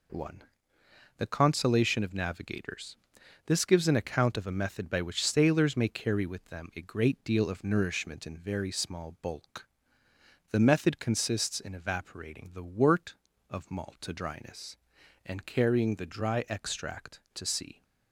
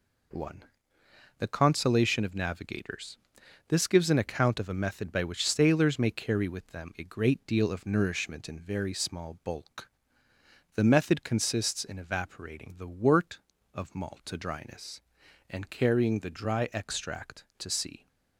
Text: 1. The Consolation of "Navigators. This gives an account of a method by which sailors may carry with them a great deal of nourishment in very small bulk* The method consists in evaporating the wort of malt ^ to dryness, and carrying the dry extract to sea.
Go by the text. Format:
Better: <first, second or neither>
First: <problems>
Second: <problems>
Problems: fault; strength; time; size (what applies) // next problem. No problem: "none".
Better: neither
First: pauses between "bulk" and "The"; noticeable; at 9.6 s; 0.84 s long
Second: pauses between "bulk" and "The"; noticeable; at 9.8 s; 0.85 s long